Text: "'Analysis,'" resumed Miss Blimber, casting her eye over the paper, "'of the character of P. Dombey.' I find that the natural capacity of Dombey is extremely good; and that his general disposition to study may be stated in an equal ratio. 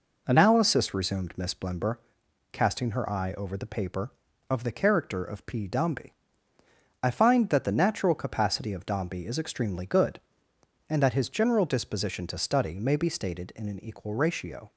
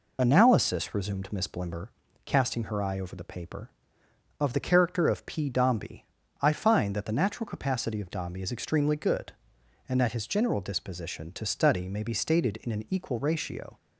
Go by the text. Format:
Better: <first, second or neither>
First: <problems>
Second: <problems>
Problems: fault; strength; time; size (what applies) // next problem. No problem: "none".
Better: first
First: none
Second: loses the start of "Analysis"; at 0.1 s; 35 ms